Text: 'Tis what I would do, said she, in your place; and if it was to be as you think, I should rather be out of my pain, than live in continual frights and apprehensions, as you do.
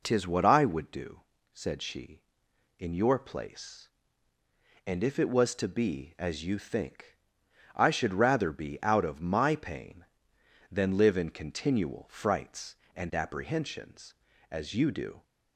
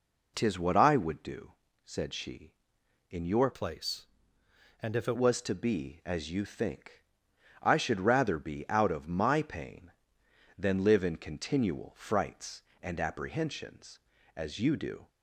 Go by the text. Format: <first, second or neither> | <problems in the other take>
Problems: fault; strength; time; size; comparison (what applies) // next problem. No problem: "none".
first | changes voice from "place" to "it"; from 3.5 to 5.1 s; 1.6 s long